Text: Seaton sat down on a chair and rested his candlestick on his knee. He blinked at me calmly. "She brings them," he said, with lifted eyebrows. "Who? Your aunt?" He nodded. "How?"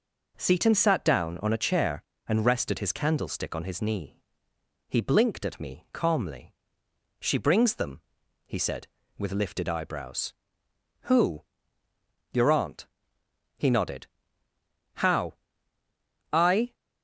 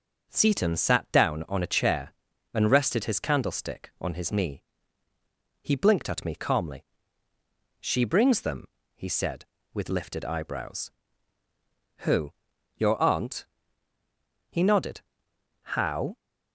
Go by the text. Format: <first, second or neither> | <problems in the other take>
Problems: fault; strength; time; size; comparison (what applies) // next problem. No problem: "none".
second | goes on to say "I"; slight; from 16.3 s on; 0.40 s long